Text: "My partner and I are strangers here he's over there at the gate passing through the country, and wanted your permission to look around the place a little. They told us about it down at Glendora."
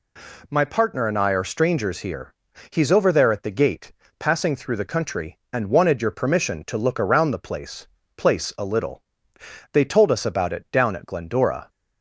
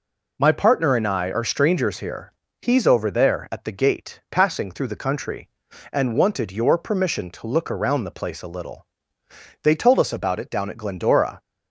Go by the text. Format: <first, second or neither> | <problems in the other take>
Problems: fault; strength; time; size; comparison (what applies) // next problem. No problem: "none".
second | pauses between "here" and "he's"; at 2.3 s; 0.38 s long; slight in the second // pauses between "gate" and "passing"; slight; at 3.9 s; 0.26 s long // says "place" twice; at 8.1 s